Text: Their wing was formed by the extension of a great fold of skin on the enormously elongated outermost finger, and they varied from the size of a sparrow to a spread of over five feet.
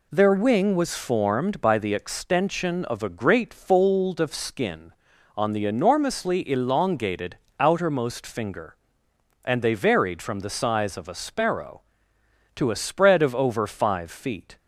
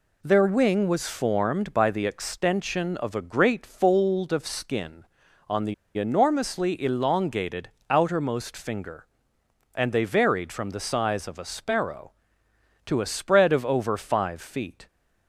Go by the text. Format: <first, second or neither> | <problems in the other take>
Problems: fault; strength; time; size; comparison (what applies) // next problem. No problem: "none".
first | pauses between "the" and "enormously"; slight; at 5.7 s; 0.23 s long // pauses between "elongated" and "outermost"; slight; at 7.6 s; 0.20 s long; slight in the first